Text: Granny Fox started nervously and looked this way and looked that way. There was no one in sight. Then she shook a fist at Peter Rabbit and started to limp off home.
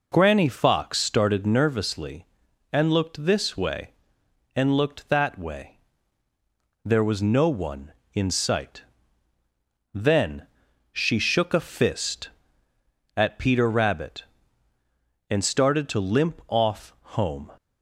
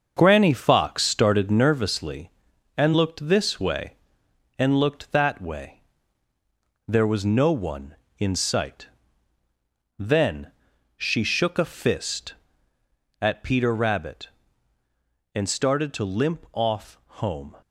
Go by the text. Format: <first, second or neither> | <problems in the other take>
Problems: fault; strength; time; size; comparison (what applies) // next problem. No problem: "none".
first | gets quieter; noticeable; throughout; 6 dB // pauses between "Then" and "she"; at 10.5 s; 0.44 s long; also in the first // pauses between "off" and "home"; slight; at 16.9 s; 0.22 s long; slight in the first